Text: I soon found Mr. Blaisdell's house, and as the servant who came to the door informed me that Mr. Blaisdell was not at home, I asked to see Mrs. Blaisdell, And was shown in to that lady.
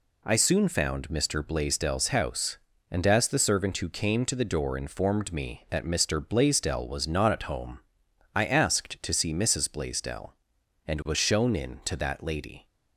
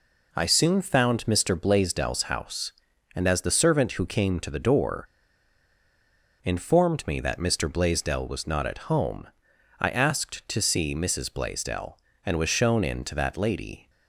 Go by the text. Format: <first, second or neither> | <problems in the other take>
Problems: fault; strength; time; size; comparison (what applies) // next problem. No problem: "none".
first | pauses between "door" and "informed"; strong; at 5.0 s; 1.3 s long